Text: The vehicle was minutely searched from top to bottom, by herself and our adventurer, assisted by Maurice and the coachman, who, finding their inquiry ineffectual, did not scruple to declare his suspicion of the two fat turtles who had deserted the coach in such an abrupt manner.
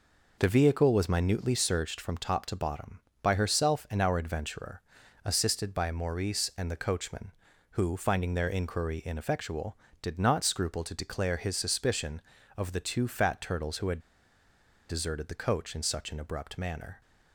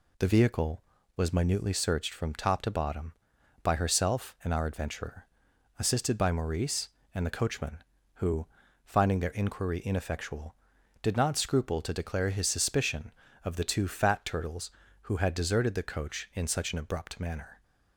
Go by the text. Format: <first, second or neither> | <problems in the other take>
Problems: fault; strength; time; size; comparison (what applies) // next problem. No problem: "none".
second | pauses between "had" and "deserted"; noticeable; at 13.9 s; 0.90 s long